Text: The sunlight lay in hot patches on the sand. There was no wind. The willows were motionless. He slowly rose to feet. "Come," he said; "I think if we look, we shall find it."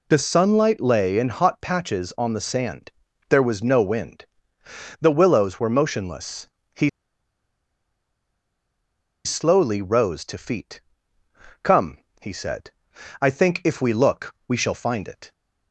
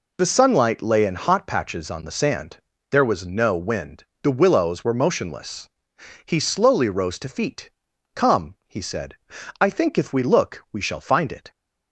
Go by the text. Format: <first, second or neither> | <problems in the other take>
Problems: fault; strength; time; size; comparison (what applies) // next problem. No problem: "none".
second | pauses between "He" and "slowly"; strong; at 6.8 s; 2.3 s long